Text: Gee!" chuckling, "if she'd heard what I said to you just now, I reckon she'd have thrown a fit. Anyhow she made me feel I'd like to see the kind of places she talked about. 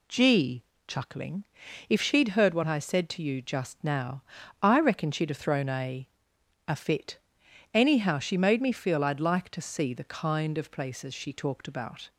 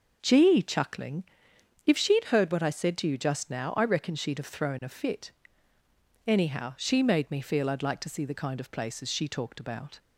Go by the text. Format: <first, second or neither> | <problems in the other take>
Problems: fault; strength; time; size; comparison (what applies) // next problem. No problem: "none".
second | says "a" twice; at 6.6 s